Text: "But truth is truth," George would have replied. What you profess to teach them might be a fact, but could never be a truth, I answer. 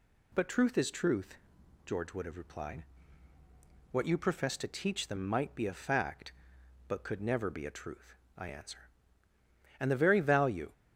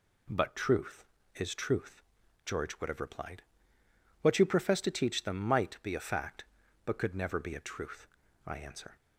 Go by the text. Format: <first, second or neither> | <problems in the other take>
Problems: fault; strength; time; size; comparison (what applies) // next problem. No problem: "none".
second | goes on to say "And the very value"; noticeable; from 9.8 s on; 0.92 s long